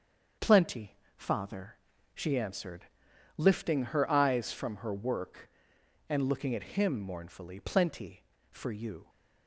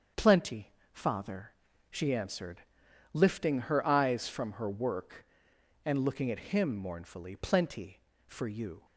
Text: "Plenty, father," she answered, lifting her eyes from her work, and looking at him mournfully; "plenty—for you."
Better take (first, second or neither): neither